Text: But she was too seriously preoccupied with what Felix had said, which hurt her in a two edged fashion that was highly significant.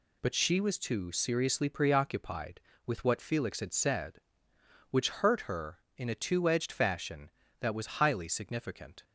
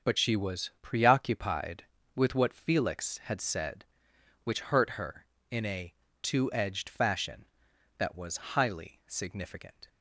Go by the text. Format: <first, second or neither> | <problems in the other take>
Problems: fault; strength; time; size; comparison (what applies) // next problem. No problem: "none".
first | starts louder than the rest; until 1.1 s; 7 dB // skips "too seriously"; at 0.7 s // pauses between "a" and "two"; slight; at 5.9 s; 0.30 s long